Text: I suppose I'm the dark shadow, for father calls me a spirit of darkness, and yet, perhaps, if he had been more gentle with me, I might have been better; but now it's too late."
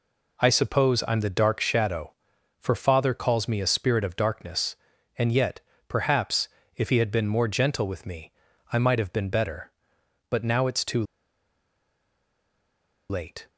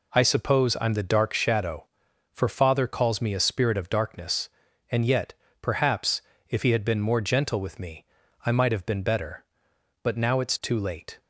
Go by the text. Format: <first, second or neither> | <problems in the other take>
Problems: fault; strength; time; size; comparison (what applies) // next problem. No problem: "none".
second | pauses between "too" and "late"; strong; at 11.0 s; 2.0 s long